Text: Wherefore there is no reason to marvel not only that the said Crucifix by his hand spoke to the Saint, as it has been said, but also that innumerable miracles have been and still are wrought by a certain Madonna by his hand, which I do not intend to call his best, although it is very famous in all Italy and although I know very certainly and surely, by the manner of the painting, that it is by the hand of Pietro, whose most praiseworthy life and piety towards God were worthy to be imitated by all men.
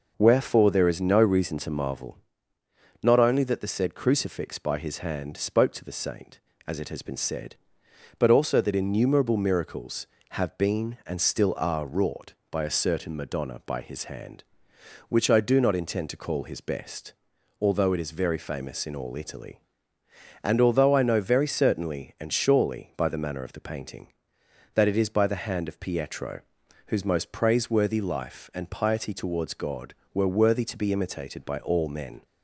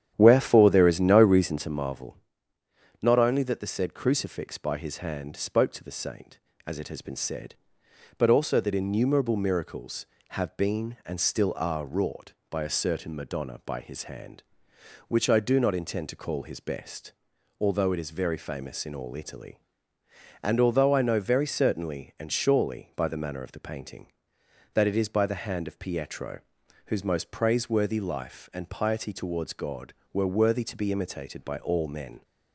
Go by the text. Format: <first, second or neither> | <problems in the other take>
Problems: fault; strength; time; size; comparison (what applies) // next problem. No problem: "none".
first | starts louder than the rest; strong; until 1.8 s; 10 dB // pauses between "marvel" and "not"; noticeable; at 2.1 s; 0.84 s long; noticeable in the first